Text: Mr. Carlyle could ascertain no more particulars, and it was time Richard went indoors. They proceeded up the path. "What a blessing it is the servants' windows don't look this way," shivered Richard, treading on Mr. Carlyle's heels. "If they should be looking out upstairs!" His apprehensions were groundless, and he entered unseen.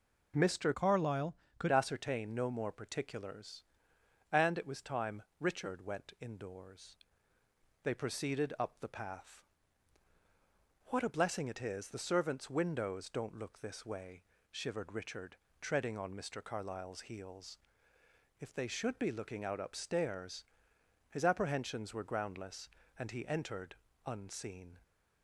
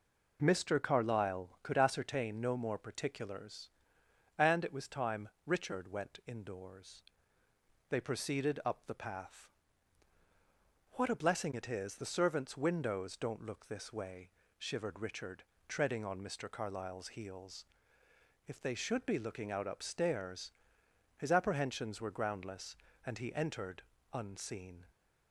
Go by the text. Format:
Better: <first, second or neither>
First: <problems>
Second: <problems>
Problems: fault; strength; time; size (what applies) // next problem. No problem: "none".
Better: second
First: changes voice from "Carlyle" to "could"; from 0.7 to 1.7 s; 1.0 s long // pauses between "time" and "Richard"; slight; at 5.2 s; 0.16 s long // pauses between "entered" and "unseen"; slight; at 23.7 s; 0.28 s long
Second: pauses between "time" and "Richard"; slight; at 5.2 s; 0.16 s long // pauses between "entered" and "unseen"; slight; at 23.8 s; 0.28 s long